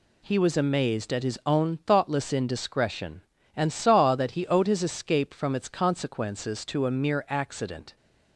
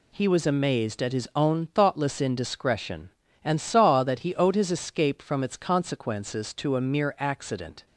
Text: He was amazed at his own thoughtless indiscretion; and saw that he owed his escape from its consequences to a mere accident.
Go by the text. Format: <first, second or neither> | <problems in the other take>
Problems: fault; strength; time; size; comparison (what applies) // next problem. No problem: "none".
neither | none